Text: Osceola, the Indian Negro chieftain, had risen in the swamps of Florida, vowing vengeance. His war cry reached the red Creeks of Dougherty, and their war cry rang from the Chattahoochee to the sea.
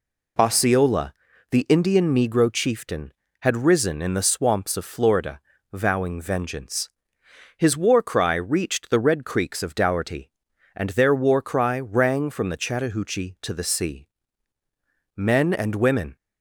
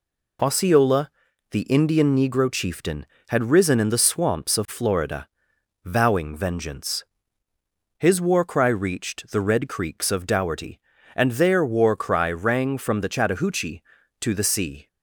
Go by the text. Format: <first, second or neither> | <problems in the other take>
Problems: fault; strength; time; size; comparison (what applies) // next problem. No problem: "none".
second | goes on to say "Men and women"; noticeable; from 15.1 s on; 1.0 s long